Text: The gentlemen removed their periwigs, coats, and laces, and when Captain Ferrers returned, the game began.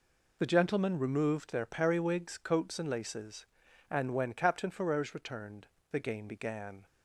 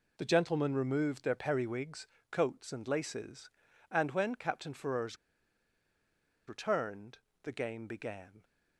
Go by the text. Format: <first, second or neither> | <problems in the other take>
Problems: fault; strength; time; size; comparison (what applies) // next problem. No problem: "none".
first | pauses between "Ferrers" and "returned"; strong; at 5.1 s; 1.3 s long